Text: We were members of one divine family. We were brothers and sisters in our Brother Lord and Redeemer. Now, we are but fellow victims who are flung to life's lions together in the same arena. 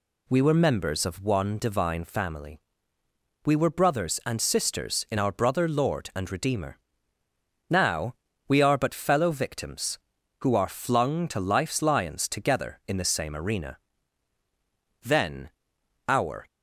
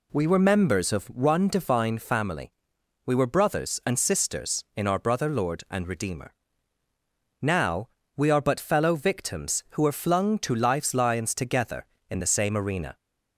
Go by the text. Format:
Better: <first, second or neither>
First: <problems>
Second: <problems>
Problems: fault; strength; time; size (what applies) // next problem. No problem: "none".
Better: second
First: goes on to say "Then our"; from 15.0 s on; 1.4 s long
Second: none